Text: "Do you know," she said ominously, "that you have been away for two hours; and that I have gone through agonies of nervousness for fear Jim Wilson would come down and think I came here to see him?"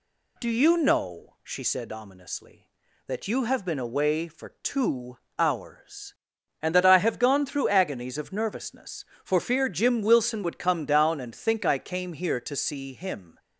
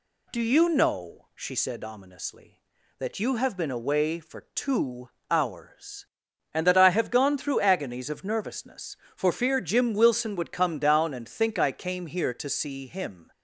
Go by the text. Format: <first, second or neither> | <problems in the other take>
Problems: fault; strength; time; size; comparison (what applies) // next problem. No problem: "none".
neither | pauses between "two" and "hours"; slight; the same in both